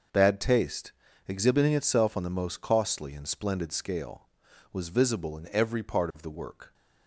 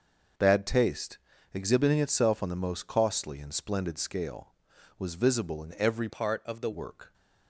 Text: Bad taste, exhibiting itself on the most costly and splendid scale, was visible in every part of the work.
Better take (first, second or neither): first